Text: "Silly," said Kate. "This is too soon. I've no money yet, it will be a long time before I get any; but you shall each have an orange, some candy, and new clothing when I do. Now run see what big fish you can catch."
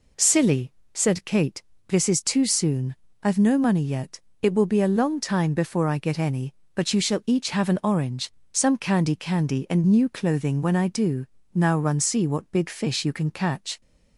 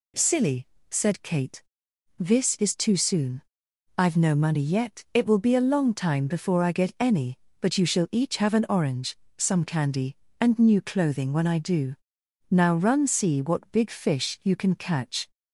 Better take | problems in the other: second | says "candy" twice; at 9.1 s

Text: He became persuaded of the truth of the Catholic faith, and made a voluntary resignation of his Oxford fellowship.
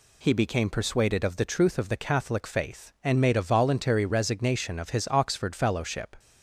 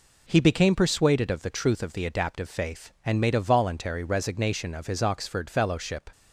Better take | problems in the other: first | says "Adaptive" for "Catholic"; at 2.0 s

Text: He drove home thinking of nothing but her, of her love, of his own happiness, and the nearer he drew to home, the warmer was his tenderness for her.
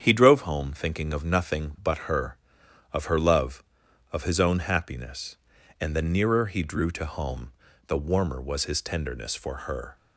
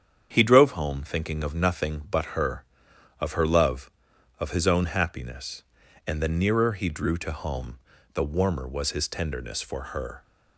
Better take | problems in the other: neither | starts louder than the rest; strong; the same in both

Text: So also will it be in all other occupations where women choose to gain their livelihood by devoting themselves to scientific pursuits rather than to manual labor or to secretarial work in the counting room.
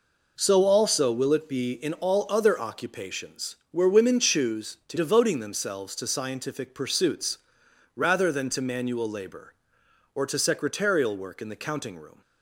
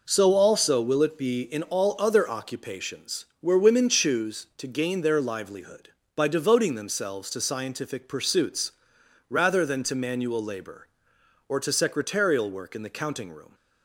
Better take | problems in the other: second | skips "gain their livelihood by"; at 4.9 s // pauses between "pursuits" and "rather"; noticeable; at 7.3 s; 0.60 s long; noticeable in the second

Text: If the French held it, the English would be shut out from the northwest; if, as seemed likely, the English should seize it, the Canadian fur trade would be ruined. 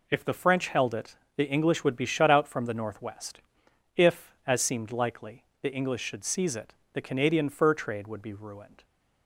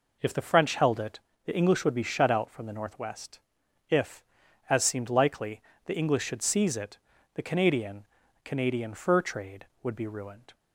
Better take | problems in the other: first | says "Canadian" twice; at 8.4 s

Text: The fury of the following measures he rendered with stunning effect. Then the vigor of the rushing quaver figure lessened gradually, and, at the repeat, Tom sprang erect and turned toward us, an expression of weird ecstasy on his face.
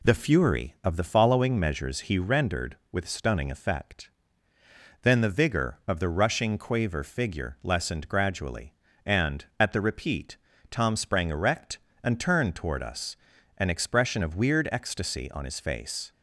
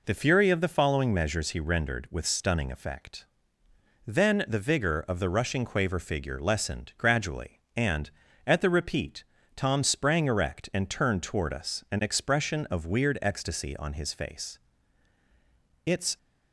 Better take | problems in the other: first | goes on to say "It's"; slight; from 15.8 s on; 0.32 s long

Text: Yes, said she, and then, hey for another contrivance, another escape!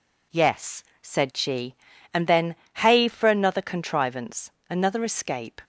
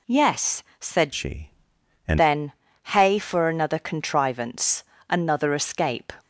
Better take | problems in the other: first | changes voice from "she" to "and"; from 1.1 to 2.1 s; 1.0 s long

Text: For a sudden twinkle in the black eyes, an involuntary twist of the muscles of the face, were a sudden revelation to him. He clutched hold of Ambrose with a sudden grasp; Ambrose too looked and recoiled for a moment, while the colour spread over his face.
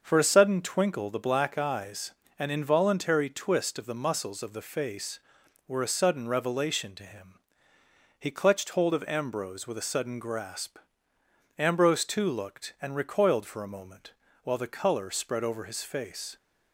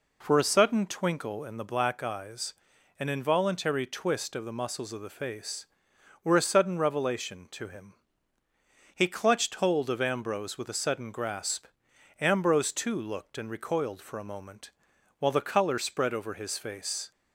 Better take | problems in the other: second | starts louder than the rest; until 1.0 s; 6.5 dB // skips "in"; at 1.1 s

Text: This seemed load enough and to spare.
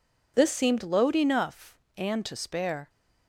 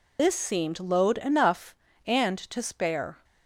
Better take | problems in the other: first | loses the start of "This"; at 0.1 s; 80 ms

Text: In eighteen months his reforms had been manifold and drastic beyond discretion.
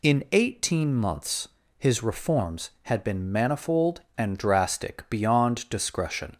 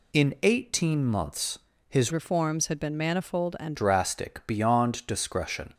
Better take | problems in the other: first | pauses between "months" and "his"; slight; at 1.5 s; 0.30 s long; slight in the first // changes voice from "reforms" to "and"; from 2.1 to 3.7 s; 1.6 s long

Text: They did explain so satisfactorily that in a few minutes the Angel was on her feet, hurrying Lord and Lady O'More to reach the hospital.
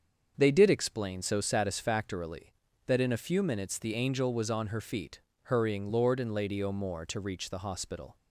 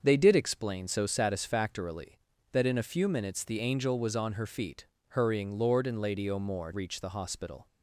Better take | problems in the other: first | starts louder than the rest; until 1.0 s; 6.5 dB; also in the first // skips "to"; at 6.7 s

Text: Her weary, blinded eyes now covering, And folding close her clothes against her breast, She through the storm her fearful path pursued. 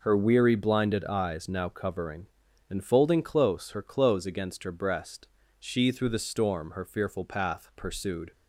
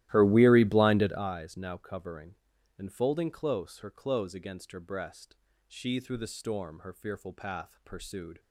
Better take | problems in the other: first | starts louder than the rest; strong; until 1.3 s; 14.5 dB

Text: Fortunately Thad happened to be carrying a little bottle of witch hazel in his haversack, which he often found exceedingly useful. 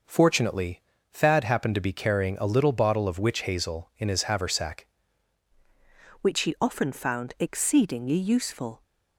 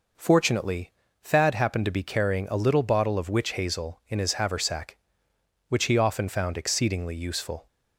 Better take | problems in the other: second | pauses between "Fortunately" and "Thad"; slight; at 0.8 s; 0.30 s long; slight in the second // changes voice at "which"; from 6.2 s on; 2.6 s long

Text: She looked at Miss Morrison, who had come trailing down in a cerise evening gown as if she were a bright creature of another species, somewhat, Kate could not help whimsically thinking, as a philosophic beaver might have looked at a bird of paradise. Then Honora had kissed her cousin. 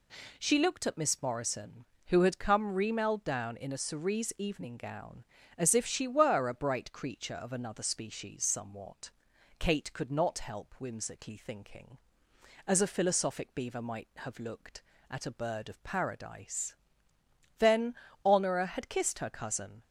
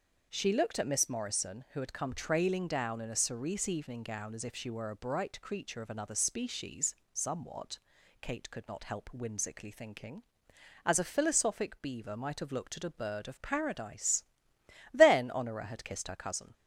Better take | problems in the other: second | says "remailed" for "trailing"; at 2.7 s // pauses between "Then" and "Honora"; slight; at 17.9 s; 0.30 s long

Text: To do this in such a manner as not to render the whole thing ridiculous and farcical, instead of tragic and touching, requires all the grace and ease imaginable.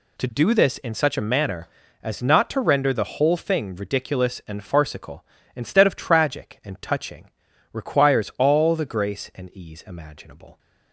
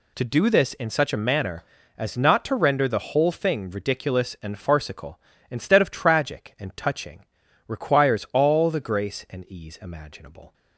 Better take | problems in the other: neither | none

